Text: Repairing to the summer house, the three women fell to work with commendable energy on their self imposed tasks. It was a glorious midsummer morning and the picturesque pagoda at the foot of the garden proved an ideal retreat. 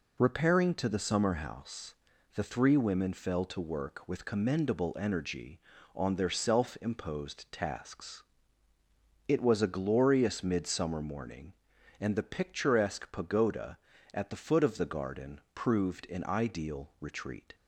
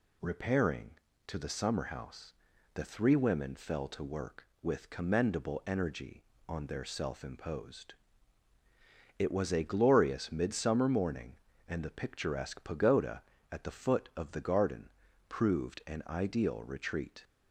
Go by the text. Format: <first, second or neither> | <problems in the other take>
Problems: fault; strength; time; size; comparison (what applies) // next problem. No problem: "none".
first | skips "tasks"; at 8.5 s // pauses between "garden" and "proved"; at 14.8 s; 0.40 s long; slight in the first